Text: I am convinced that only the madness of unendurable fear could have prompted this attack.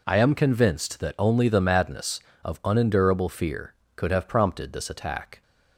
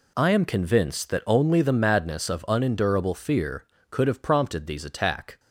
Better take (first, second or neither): first